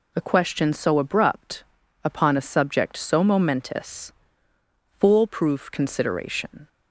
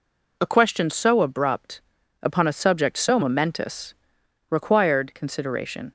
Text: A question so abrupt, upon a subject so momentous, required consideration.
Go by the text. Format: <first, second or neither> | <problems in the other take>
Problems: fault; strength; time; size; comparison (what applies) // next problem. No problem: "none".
second | says "foolproof" for "required"; at 4.9 s